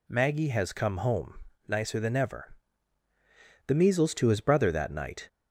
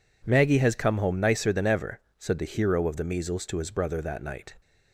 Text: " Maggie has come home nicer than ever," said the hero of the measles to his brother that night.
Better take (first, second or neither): second